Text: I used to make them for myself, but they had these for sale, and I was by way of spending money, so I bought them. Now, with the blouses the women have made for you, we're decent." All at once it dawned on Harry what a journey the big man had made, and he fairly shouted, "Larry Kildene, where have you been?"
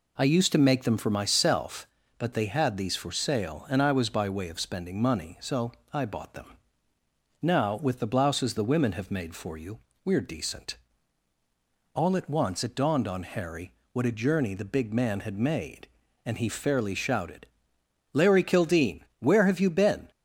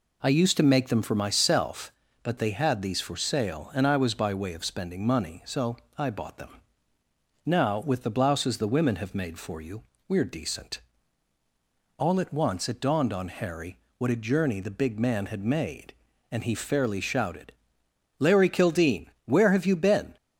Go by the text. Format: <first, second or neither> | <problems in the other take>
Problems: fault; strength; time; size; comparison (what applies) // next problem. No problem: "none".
neither | pauses between "so" and "I"; slight; the same in both // pauses between "Harry" and "what"; slight; the same in both